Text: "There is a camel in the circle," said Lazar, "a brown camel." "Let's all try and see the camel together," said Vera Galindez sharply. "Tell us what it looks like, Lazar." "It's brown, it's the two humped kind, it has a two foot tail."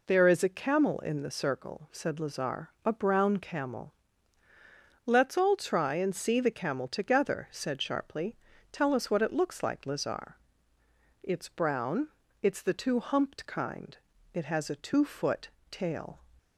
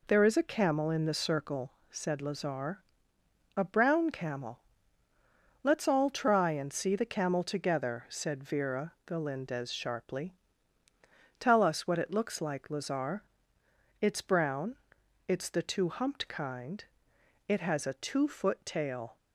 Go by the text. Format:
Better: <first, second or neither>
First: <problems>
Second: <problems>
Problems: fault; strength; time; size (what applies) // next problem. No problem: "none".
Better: second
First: skips "Vera Galindez"; at 7.8 s // pauses between "foot" and "tail"; slight; at 15.4 s; 0.22 s long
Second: none